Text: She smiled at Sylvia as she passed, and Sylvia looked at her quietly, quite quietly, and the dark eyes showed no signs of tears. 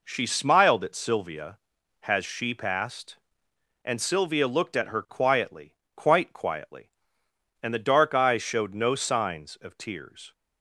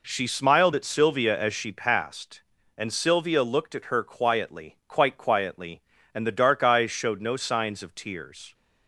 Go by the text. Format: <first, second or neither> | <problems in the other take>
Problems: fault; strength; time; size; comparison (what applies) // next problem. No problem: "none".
second | says "has" for "as"; at 2.0 s